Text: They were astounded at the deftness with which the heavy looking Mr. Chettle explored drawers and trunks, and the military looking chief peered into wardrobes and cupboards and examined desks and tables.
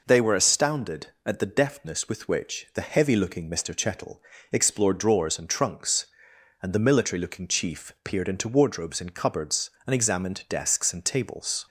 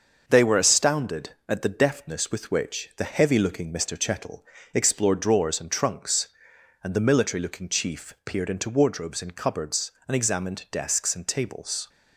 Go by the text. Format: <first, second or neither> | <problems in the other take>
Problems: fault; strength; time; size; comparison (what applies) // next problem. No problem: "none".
first | gets quieter; throughout; 4 dB // pauses between "Chettle" and "explored"; slight; at 4.4 s; 0.29 s long; slight in the first